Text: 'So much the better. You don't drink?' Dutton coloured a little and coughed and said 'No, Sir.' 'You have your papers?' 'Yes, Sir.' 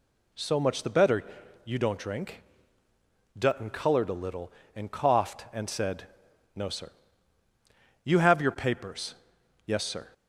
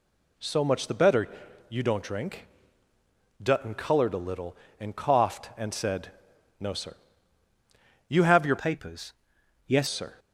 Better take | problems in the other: first | pauses between "said" and "No"; noticeable; at 6.1 s; 0.50 s long; noticeable in the first // changes voice from "papers" to "Yes"; from 8.5 to 9.8 s; 1.3 s long

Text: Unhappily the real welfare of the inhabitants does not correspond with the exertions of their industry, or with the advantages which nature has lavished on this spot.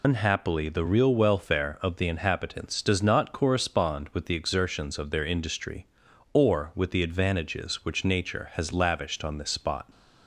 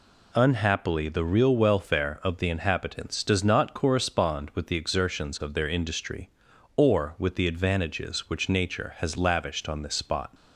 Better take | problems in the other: second | loses the start of "Unhappily"; at 0.0 s; 100 ms

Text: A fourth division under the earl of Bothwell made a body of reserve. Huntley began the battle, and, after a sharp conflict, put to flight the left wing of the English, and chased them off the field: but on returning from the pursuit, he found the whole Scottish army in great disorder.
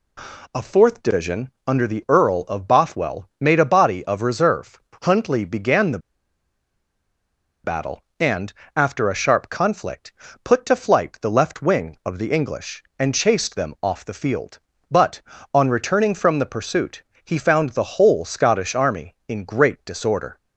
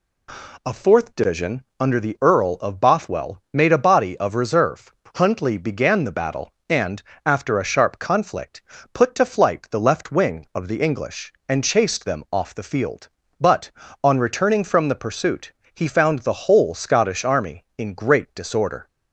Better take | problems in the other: second | pauses between "the" and "battle"; strong; at 5.9 s; 1.6 s long

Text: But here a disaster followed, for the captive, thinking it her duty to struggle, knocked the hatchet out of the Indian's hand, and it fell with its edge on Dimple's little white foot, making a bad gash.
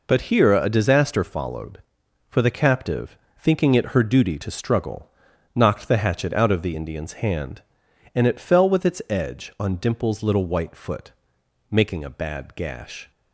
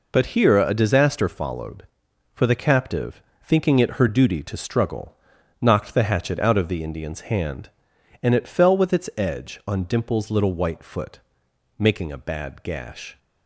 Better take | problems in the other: neither | none

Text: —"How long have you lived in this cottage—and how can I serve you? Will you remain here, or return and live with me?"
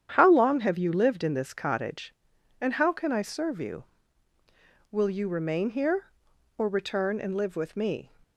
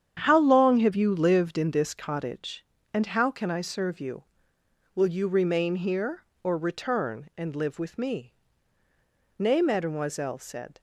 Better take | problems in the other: first | starts louder than the rest; strong; until 1.2 s; 8.5 dB; strong in the first // goes on to say "Nay mademoiselle said"; from 9.3 s on; 1.4 s long

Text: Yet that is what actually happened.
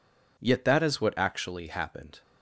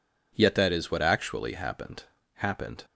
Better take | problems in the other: first | says "happened" twice; at 2.3 s

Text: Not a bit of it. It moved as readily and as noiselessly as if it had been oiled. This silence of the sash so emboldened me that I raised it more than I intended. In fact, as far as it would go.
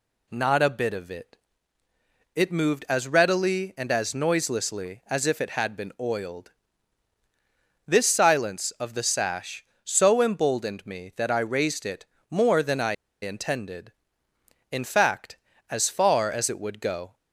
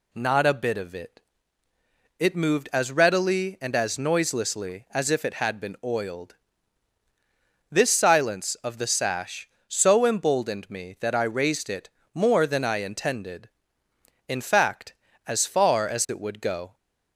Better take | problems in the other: second | pauses between "it" and "more"; slight; at 12.0 s; 0.26 s long; slight in the second // pauses between "I" and "intended"; slight; at 12.9 s; 0.28 s long

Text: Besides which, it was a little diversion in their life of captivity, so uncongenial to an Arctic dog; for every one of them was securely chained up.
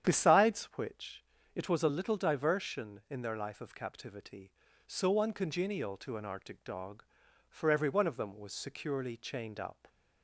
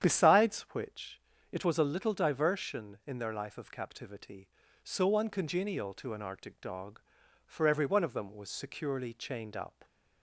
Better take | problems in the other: neither | starts louder than the rest; strong; the same in both

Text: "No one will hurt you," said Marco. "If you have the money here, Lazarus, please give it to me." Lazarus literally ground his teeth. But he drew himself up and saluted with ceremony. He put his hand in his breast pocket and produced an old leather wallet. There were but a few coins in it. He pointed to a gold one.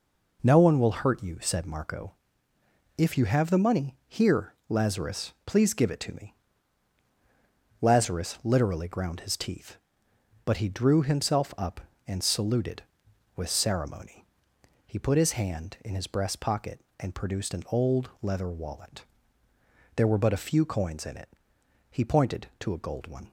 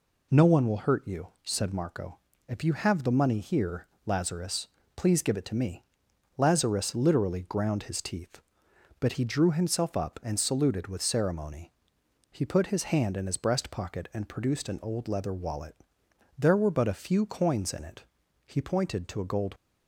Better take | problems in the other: first | stops before "one"; at 19.5 s

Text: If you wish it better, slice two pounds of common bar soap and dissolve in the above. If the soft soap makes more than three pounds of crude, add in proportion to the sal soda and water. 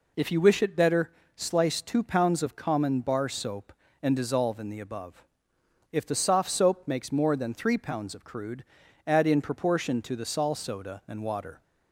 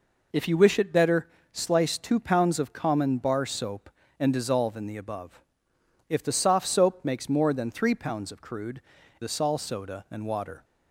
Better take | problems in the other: first | skips "add in proportion to"; at 9.0 s

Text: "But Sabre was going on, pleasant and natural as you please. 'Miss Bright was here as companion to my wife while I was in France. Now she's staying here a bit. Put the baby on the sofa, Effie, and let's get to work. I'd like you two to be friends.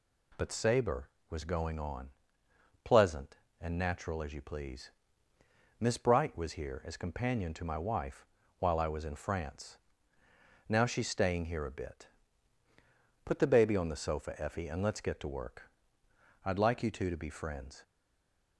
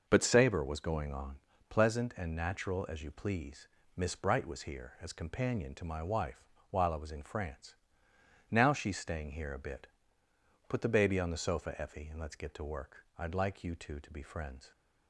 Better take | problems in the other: second | pauses between "wife" and "while"; slight; at 8.2 s; 0.34 s long; slight in the second // stays silent after the last word; slight; from 17.8 s on; 0.7 s long

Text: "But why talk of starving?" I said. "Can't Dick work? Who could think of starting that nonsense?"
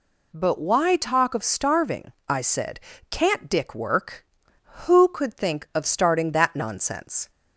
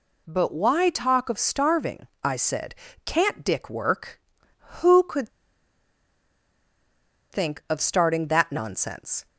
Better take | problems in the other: first | pauses between "could" and "think"; strong; at 5.2 s; 2.0 s long

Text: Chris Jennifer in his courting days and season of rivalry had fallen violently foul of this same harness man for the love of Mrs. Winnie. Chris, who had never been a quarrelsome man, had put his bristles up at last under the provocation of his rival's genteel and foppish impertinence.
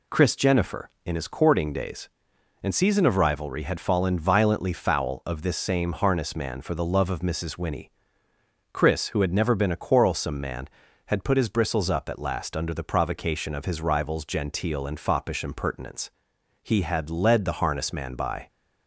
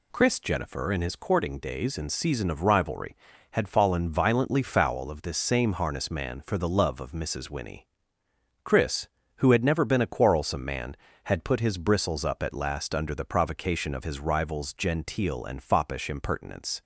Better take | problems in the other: second | goes on to say "He had led the harness man by"; strong; from 16.6 s on; 1.8 s long

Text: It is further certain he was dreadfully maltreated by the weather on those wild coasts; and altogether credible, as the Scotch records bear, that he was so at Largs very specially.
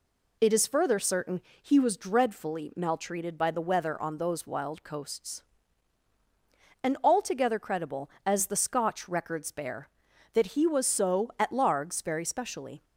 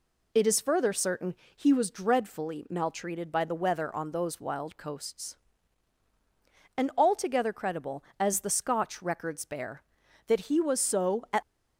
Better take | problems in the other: first | pauses between "certain" and "he"; slight; at 1.3 s; 0.20 s long; slight in the first // stops before "Largs very specially"; at 11.4 s

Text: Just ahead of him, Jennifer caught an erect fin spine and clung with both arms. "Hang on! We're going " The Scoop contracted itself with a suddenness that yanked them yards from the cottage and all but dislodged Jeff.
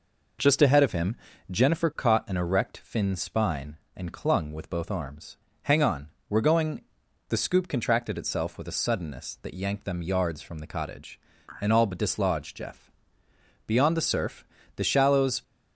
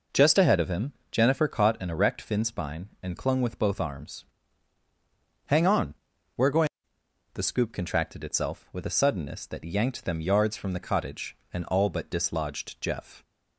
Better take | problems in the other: second | goes on to say "Beyond the surf the shallows"; strong; from 13.6 s on; 1.7 s long

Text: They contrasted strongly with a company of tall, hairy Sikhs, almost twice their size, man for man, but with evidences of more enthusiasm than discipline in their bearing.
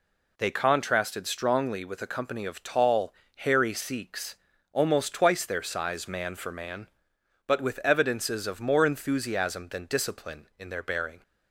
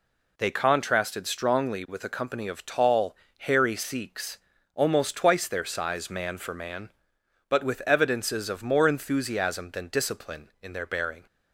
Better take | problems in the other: neither | none

